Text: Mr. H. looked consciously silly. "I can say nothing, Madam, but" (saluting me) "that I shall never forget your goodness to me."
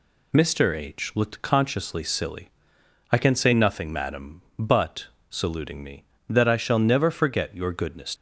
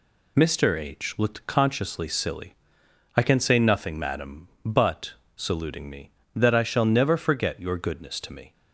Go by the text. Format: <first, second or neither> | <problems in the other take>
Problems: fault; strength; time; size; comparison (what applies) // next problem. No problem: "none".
second | stops before "to me"; at 8.1 s